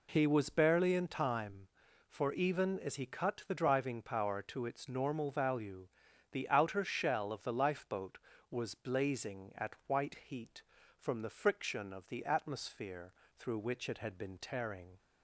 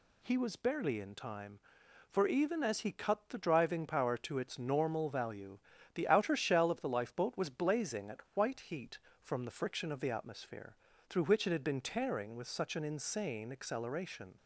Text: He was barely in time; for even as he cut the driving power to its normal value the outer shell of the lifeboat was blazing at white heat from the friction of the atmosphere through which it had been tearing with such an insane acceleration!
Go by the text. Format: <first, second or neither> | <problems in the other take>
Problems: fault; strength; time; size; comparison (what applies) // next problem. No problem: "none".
second | pauses between "value" and "the"; noticeable; at 5.8 s; 0.46 s long; slight in the second // pauses between "atmosphere" and "through"; slight; at 13.1 s; 0.24 s long; slight in the second // stops before "with such an insane acceleration"; at 14.9 s